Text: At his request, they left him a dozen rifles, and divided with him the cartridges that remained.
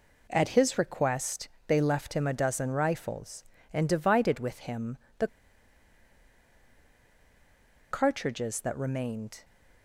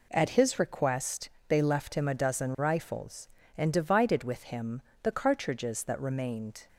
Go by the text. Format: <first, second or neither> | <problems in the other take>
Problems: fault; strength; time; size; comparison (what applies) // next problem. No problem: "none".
second | pauses between "him" and "the"; slight; at 4.9 s; 0.20 s long; slight in the second // pauses between "the" and "cartridges"; strong; at 5.2 s; 2.6 s long